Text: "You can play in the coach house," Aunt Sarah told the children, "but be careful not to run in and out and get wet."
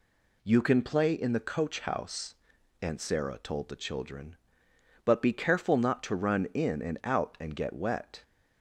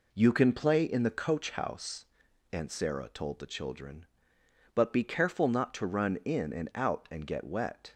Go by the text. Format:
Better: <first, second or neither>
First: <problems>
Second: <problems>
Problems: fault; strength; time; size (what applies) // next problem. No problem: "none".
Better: first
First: none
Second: starts louder than the rest; until 1.6 s; 3.5 dB